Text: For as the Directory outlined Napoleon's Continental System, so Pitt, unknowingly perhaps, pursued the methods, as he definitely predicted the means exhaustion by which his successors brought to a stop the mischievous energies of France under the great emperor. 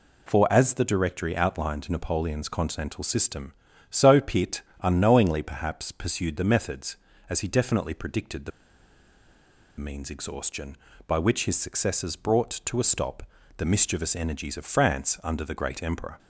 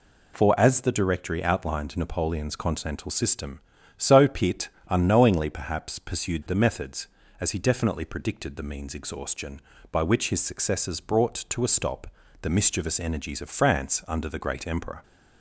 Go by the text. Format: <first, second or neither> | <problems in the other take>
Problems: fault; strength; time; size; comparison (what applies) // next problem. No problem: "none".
second | pauses between "the" and "means"; strong; at 8.5 s; 1.2 s long // pauses between "stop" and "the"; slight; at 13.2 s; 0.36 s long; slight in the second